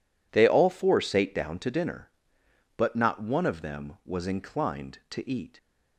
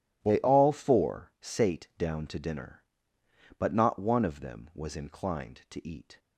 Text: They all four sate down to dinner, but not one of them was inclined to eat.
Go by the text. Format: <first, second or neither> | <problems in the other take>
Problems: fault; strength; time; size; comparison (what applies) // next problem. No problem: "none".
neither | none